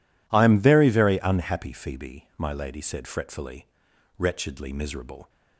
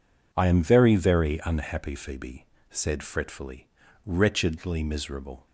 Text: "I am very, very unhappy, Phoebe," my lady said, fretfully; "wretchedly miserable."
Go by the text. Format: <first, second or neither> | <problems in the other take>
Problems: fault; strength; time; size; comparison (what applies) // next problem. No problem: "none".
first | skips "my lady"; at 2.5 s